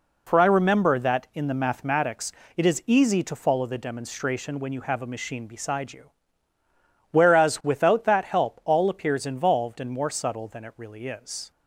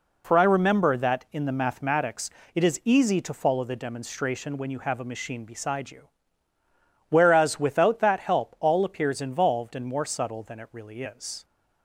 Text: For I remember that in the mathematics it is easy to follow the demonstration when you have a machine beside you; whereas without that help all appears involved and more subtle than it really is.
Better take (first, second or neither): neither